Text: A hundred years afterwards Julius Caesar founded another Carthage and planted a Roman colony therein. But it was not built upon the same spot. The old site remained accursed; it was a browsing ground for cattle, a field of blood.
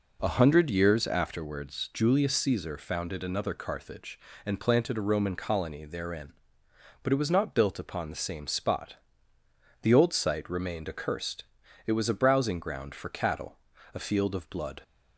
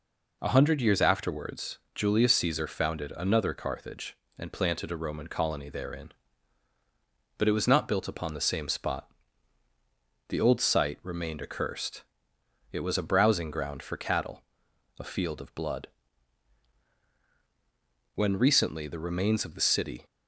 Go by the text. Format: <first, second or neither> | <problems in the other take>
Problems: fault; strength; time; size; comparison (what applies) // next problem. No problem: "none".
first | pauses between "afterwards" and "Julius"; slight; at 1.7 s; 0.16 s long // goes on to say "When recently the remains of the city"; strong; from 18.1 s on; 1.9 s long